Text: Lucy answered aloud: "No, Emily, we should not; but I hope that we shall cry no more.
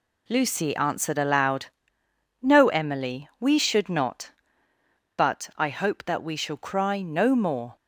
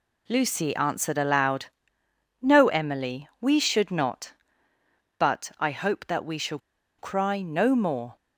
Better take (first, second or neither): first